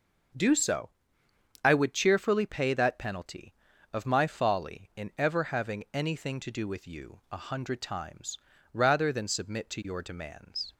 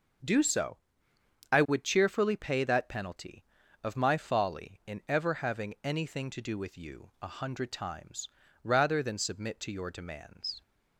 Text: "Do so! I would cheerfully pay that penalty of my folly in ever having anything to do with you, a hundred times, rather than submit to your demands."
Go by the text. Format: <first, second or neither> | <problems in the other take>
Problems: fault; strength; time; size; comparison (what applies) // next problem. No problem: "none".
neither | starts louder than the rest; the same in both